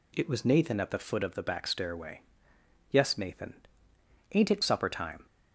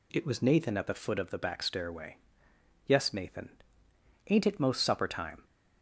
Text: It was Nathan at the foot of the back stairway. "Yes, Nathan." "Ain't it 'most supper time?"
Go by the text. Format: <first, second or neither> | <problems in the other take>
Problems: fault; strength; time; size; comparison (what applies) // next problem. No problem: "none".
second | skips "most"; at 4.6 s